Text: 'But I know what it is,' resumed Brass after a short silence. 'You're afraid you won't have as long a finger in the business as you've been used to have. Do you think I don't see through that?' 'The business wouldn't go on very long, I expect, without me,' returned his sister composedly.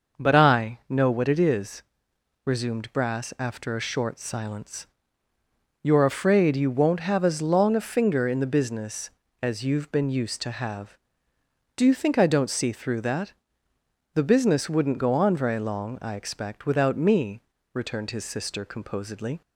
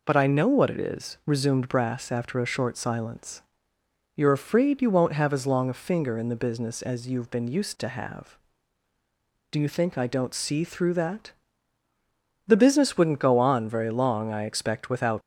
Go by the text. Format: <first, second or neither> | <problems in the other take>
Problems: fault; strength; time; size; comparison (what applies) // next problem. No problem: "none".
first | stops before "me returned his sister composedly"; at 15.2 s